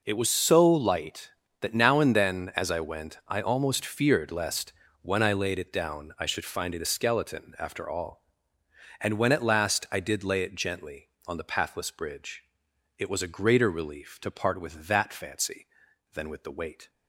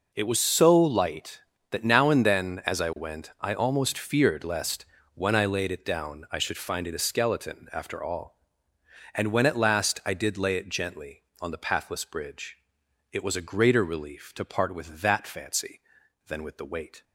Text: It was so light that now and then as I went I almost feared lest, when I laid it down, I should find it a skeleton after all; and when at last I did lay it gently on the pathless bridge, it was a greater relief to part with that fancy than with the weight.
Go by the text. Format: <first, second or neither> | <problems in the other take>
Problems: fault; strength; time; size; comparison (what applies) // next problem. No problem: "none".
neither | none